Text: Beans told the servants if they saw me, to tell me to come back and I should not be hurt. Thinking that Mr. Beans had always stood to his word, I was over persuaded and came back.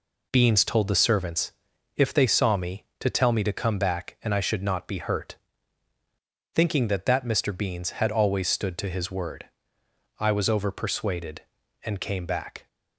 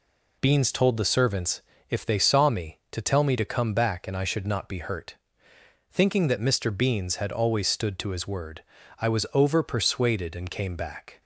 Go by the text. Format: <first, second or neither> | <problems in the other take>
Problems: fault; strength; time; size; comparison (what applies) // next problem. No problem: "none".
second | pauses between "servants" and "if"; noticeable; at 1.5 s; 0.46 s long; slight in the second // says "that" twice; at 7.0 s